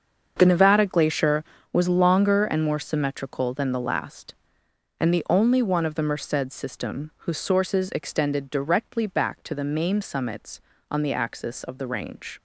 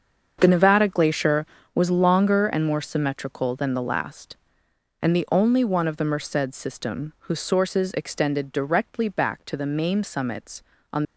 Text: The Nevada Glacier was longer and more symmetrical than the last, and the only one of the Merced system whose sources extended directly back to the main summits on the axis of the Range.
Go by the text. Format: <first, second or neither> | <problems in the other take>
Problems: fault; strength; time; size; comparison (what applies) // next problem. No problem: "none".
first | starts louder than the rest; until 1.4 s; 7 dB; also in the first // stops before "the axis of the Range"; at 11.0 s